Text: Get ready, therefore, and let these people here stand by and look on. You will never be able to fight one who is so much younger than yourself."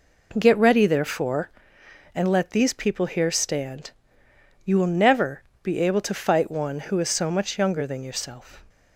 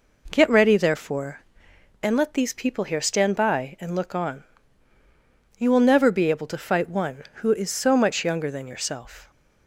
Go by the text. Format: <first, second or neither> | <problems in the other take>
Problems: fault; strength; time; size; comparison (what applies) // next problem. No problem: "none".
second | skips "by and look on"; at 4.2 s // pauses between "never" and "be"; slight; at 5.4 s; 0.20 s long